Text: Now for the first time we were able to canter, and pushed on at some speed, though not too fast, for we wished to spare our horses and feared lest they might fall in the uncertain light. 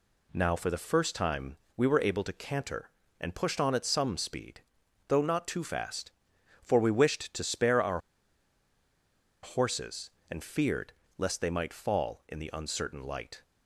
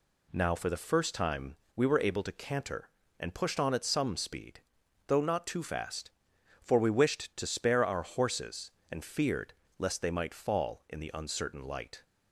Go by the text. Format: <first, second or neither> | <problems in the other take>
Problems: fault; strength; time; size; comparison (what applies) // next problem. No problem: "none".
second | pauses between "time" and "we"; slight; at 1.5 s; 0.20 s long; slight in the second // pauses between "our" and "horses"; strong; at 8.0 s; 1.4 s long // pauses between "feared" and "lest"; slight; at 10.9 s; 0.24 s long; slight in the second